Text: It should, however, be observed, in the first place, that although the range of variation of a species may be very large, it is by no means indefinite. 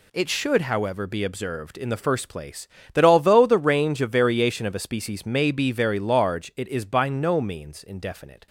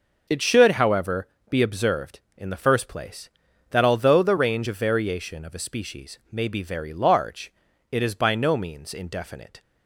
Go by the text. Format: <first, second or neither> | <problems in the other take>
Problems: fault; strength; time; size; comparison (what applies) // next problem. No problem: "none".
neither | none